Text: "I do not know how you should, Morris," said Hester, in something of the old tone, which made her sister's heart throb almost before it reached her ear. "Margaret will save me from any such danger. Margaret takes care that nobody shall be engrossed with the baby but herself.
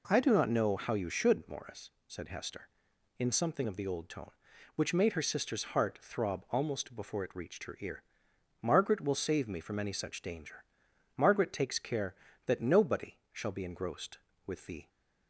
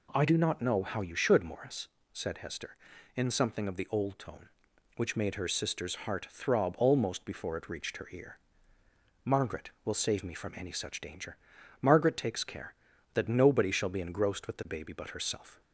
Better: second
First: pauses between "nobody" and "shall"; slight; at 13.1 s; 0.16 s long // stops before "baby but herself"; at 14.8 s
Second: none

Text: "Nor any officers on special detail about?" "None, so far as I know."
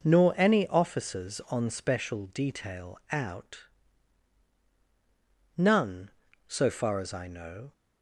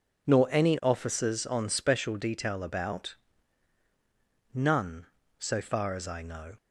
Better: second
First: says "out" for "about"; at 3.1 s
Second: none

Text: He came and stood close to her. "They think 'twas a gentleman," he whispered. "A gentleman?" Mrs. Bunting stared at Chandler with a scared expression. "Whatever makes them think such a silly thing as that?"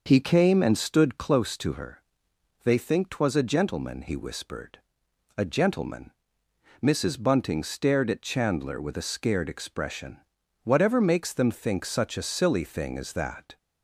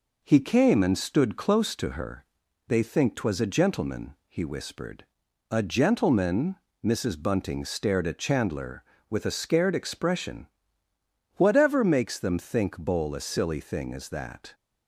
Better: first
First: none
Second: says "bowl" for "such"; at 12.7 s

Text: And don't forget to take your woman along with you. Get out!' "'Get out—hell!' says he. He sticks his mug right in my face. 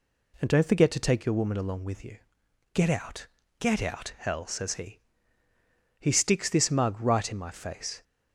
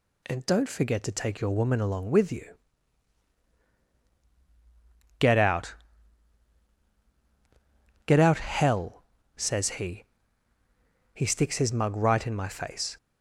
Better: second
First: says "this" for "his"; at 6.4 s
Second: none

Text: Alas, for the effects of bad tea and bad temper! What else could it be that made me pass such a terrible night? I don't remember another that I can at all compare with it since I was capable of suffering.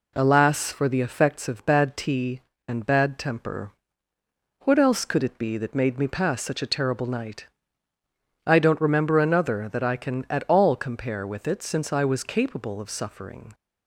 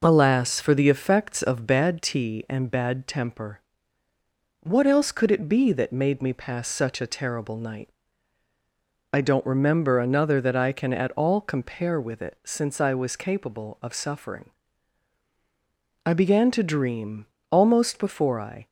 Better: first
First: none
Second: goes on to say "I began to dream almost before I"; strong; from 16.0 s on; 2.6 s long

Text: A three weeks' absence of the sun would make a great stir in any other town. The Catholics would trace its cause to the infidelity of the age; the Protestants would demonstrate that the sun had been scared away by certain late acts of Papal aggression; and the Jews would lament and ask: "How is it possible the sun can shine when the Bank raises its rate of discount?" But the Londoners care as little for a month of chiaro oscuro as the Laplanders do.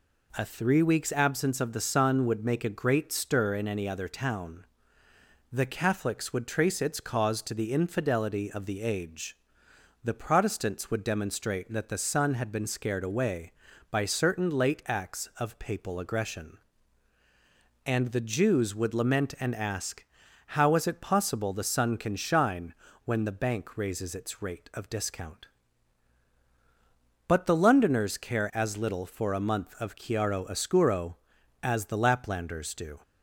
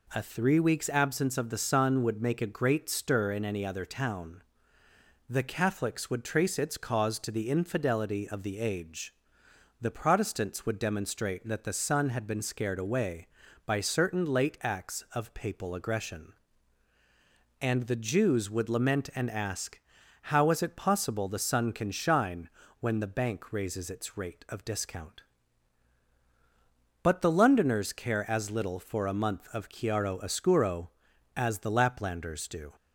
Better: neither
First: pauses between "shine" and "when"; slight; at 22.7 s; 0.30 s long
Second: pauses between "shine" and "when"; slight; at 22.4 s; 0.30 s long

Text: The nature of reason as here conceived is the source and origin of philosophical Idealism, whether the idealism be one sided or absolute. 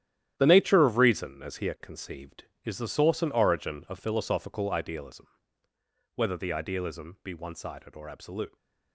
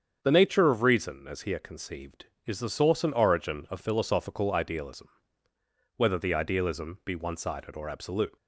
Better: second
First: gets quieter; strong; throughout; 10.5 dB // starts louder than the rest; strong; until 1.3 s; 11 dB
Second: starts louder than the rest; strong; until 1.2 s; 7.5 dB

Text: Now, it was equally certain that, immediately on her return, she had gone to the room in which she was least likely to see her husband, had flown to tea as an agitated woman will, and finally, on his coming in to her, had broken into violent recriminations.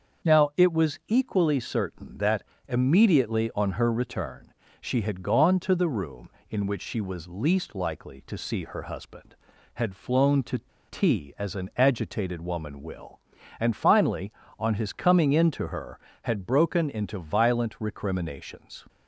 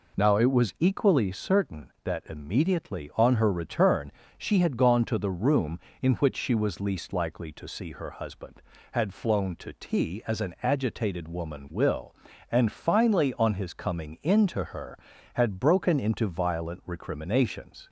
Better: second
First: starts louder than the rest; until 1.3 s; 6.5 dB // pauses between "to" and "tea"; slight; at 10.6 s; 0.29 s long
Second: none

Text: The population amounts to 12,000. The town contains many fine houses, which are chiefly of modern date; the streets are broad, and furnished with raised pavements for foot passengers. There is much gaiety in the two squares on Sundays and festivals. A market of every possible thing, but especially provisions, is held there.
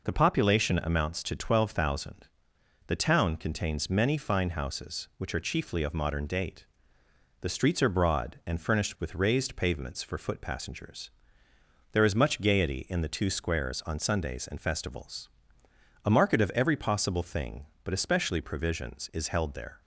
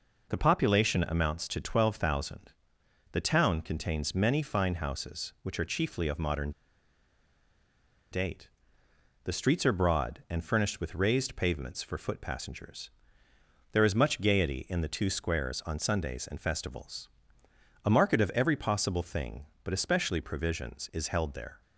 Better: first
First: none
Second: pauses between "modern" and "date"; strong; at 6.5 s; 1.6 s long

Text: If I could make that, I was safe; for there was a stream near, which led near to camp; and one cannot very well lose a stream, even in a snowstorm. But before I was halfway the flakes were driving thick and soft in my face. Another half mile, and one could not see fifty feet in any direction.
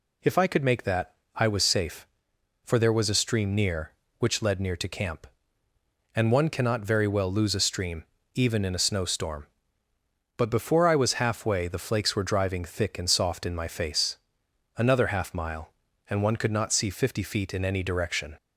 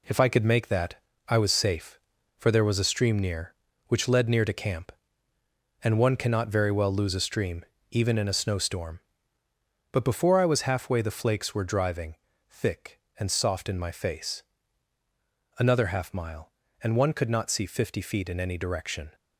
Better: first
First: none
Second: gets quieter; noticeable; throughout; 5.5 dB // pauses between "driving" and "thick"; slight; at 12.1 s; 0.34 s long

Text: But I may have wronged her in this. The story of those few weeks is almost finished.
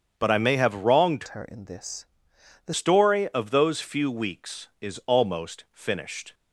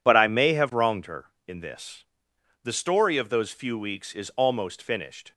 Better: second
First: starts louder than the rest; strong; until 1.1 s; 7.5 dB // changes voice from "her" to "The"; from 1.2 to 2.7 s; 1.5 s long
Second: none

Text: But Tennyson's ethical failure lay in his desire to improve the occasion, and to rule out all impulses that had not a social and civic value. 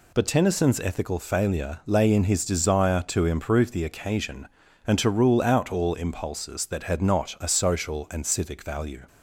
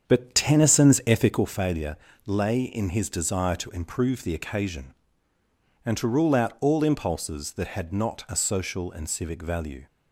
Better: first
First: none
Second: starts louder than the rest; strong; until 1.5 s; 8 dB // pauses between "failure" and "lay"; slight; at 1.9 s; 0.30 s long

